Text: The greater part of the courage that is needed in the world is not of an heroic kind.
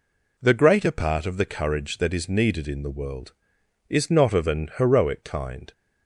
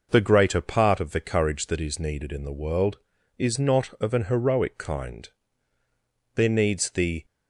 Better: first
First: none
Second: goes on to say "There needs the"; noticeable; from 6.3 s on; 0.90 s long

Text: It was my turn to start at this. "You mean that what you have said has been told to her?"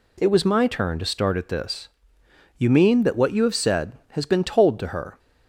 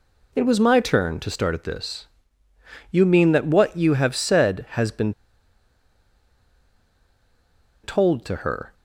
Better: first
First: none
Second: pauses between "been" and "told"; strong; at 5.1 s; 2.7 s long

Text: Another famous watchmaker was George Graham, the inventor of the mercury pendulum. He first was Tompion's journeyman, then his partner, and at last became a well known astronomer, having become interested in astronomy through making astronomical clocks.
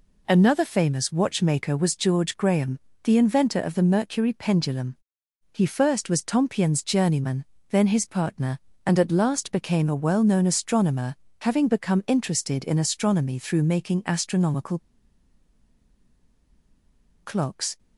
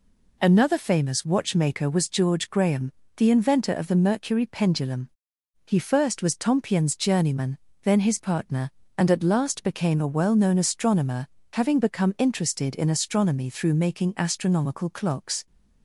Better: second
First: pauses between "astronomical" and "clocks"; strong; at 14.7 s; 2.4 s long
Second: none

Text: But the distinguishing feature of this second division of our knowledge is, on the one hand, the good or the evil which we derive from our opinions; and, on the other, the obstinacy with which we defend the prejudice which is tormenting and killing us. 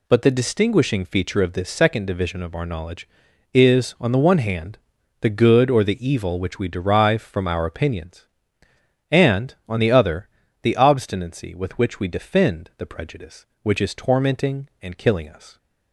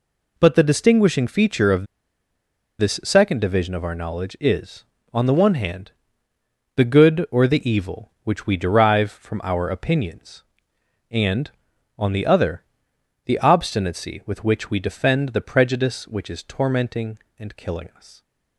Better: first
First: none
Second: pauses between "of" and "this"; noticeable; at 1.8 s; 0.93 s long

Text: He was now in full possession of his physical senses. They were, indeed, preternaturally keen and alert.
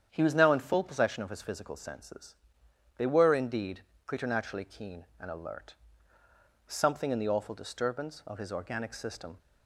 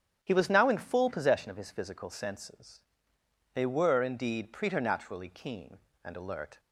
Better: second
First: starts louder than the rest; strong; until 1.1 s; 8.5 dB // goes on to say "Something in the awful disturbance of his organic system"; strong; from 6.6 s on; 2.7 s long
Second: starts louder than the rest; strong; until 1.2 s; 9 dB

